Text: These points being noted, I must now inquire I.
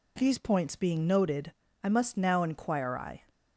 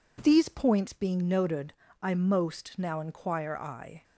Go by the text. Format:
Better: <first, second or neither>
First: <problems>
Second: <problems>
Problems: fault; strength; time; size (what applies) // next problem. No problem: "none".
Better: first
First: none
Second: says "most" for "must"; at 2.1 s